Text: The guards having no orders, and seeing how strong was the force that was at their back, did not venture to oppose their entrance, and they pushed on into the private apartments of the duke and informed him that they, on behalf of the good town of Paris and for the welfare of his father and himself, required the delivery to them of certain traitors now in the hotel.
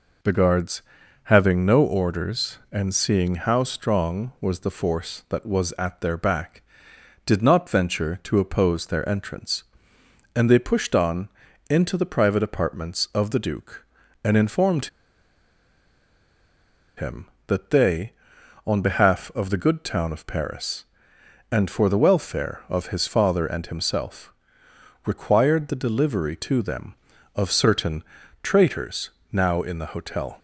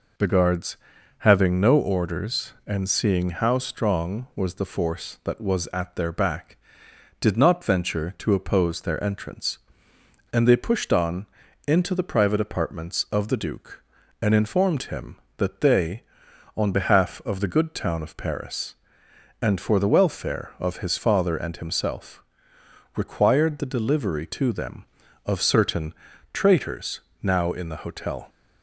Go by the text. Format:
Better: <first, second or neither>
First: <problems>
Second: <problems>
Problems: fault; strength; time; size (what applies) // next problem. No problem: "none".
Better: second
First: pauses between "guards" and "having"; at 0.8 s; 0.42 s long // pauses between "on" and "into"; at 11.2 s; 0.40 s long // pauses between "informed" and "him"; strong; at 14.8 s; 2.1 s long // pauses between "certain" and "traitors"; at 28.0 s; 0.40 s long // pauses between "traitors" and "now"; slight; at 29.1 s; 0.20 s long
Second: pauses between "guards" and "having"; at 0.7 s; 0.42 s long // pauses between "on" and "into"; at 11.2 s; 0.40 s long // pauses between "certain" and "traitors"; at 25.9 s; 0.40 s long // pauses between "traitors" and "now"; slight; at 27.0 s; 0.20 s long